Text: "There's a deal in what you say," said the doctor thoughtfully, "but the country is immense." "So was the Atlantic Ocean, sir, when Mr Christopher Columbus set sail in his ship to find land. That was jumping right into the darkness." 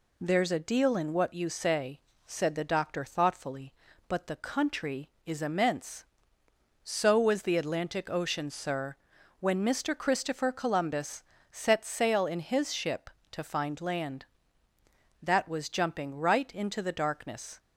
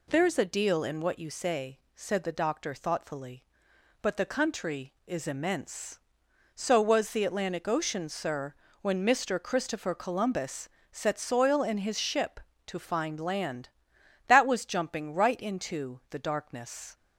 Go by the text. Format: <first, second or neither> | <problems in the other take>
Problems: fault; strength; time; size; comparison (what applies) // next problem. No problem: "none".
first | pauses between "Columbus" and "set"; slight; at 10.6 s; 0.24 s long; slight in the first // says "soil" for "sail"; at 11.1 s